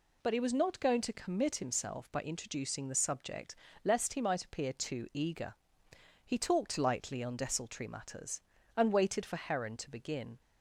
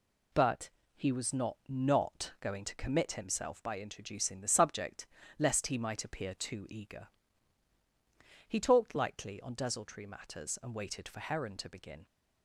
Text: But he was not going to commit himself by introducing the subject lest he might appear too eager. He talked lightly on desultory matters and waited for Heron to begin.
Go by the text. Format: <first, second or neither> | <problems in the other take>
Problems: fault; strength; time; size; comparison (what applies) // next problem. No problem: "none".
first | pauses between "But" and "he"; slight; at 0.7 s; 0.26 s long // says "not" twice; at 1.6 s // pauses between "subject" and "lest"; slight; at 5.0 s; 0.32 s long; slight in the first